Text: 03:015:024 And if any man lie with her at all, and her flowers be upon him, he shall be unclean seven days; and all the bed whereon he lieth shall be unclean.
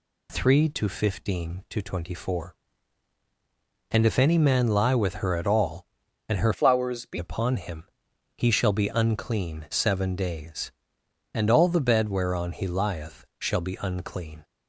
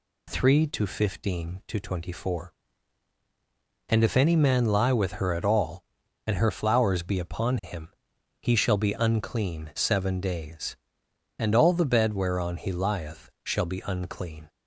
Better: second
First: changes voice from "flowers" to "be"; from 6.5 to 7.1 s; 0.6 s long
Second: none

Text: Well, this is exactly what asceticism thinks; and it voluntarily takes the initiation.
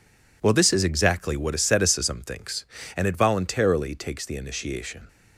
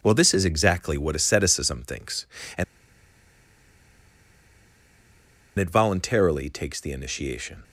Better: first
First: none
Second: pauses between "and" and "it"; strong; at 2.6 s; 2.9 s long

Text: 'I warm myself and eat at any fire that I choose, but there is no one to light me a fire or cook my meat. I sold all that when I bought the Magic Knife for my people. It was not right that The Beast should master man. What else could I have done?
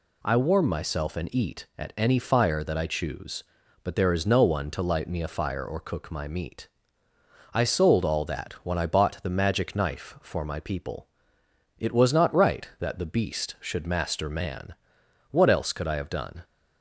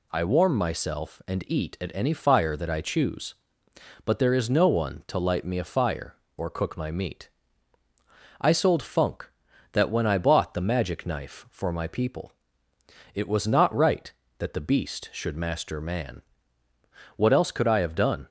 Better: first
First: none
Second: says "funk" for "all"; at 8.8 s

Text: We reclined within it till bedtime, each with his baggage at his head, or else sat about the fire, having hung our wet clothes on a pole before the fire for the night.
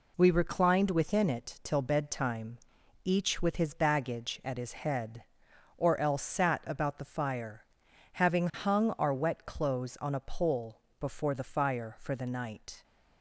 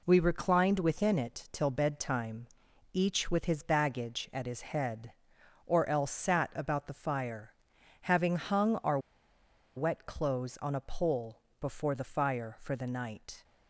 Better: first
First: pauses between "pole" and "before"; slight; at 10.8 s; 0.18 s long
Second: pauses between "our" and "wet"; noticeable; at 8.9 s; 0.78 s long // pauses between "pole" and "before"; slight; at 11.4 s; 0.18 s long

